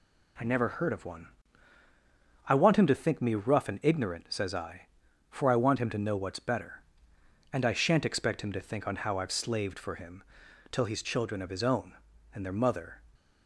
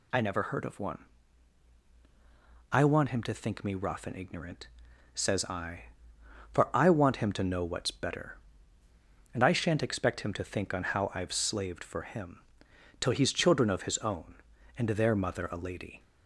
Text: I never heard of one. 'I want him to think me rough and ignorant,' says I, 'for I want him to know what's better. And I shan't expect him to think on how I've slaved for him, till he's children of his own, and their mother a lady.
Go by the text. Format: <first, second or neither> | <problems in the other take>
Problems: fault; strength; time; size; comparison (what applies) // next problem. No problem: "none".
second | stops before "a lady"; at 13.1 s